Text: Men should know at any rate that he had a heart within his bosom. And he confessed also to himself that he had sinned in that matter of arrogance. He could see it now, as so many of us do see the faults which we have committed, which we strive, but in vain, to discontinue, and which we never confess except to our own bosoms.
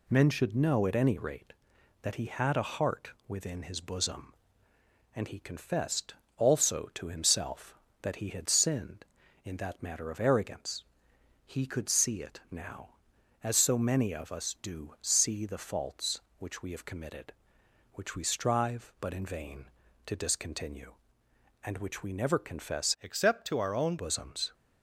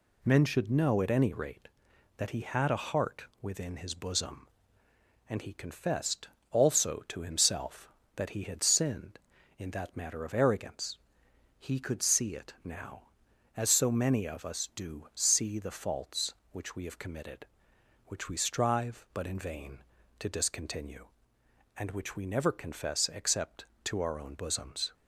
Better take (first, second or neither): second